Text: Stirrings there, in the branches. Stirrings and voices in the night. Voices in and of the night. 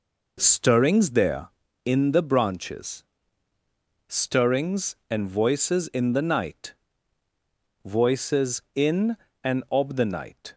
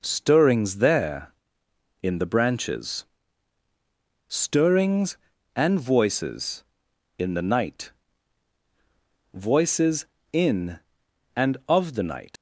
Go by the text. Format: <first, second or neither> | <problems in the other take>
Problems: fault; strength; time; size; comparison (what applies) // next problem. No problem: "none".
first | leaves "night" unfinished; at 12.3 s; 115 ms